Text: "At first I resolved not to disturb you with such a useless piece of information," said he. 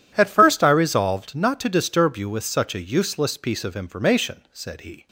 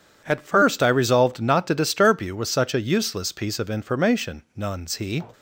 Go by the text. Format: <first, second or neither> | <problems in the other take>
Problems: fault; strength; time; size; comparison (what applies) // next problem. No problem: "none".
first | says "nuns" for "said"; at 4.5 s